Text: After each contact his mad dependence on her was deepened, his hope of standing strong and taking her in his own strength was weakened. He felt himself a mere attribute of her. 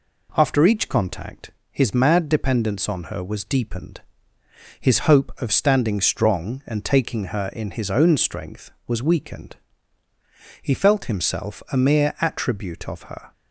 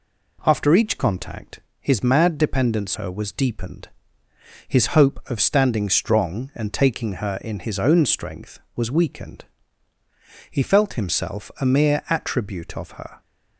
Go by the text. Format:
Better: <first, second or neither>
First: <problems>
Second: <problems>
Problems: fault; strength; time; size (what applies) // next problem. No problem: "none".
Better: first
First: pauses between "contact" and "his"; slight; at 1.5 s; 0.20 s long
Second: pauses between "contact" and "his"; slight; at 1.5 s; 0.20 s long // skips "on"; at 2.9 s